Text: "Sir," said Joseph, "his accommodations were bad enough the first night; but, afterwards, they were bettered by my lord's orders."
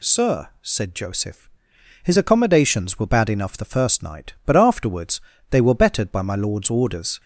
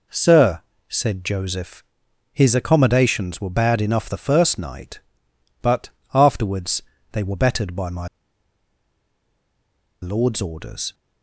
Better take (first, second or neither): first